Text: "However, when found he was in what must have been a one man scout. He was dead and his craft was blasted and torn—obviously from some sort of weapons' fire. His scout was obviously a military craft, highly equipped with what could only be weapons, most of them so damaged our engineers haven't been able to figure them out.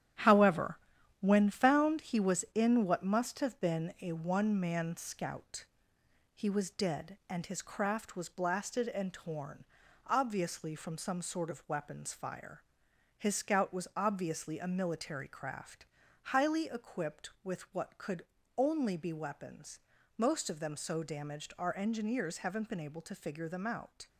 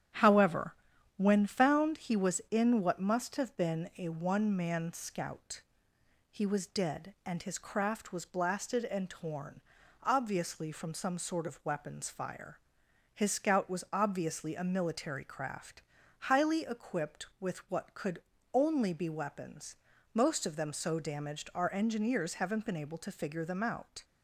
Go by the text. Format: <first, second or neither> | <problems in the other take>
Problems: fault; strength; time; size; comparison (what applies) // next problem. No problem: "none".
second | gets quieter; throughout; 6.5 dB // starts louder than the rest; strong; until 1.6 s; 10.5 dB; strong in the second // pauses between "could" and "only"; slight; at 18.2 s; 0.32 s long; slight in the second